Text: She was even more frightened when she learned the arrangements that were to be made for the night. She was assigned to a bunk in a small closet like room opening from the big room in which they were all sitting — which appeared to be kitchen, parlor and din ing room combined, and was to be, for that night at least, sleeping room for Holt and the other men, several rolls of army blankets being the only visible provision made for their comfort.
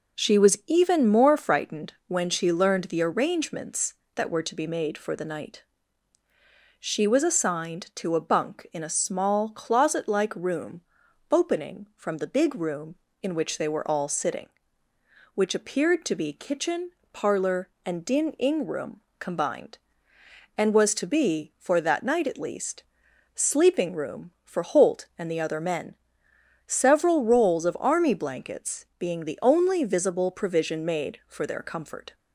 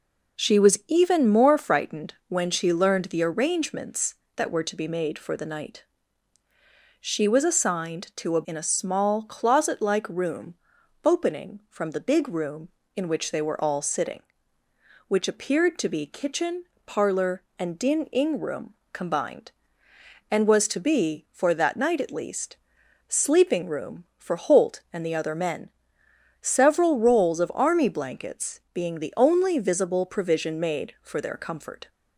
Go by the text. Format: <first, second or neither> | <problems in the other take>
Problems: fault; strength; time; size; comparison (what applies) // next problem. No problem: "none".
first | pauses between "frightened" and "when"; slight; at 2.1 s; 0.16 s long; slight in the first // skips "bunk"; at 8.4 s // pauses between "room" and "opening"; noticeable; at 10.5 s; 0.50 s long; noticeable in the first // pauses between "room" and "combined"; slight; at 18.7 s; 0.18 s long; slight in the first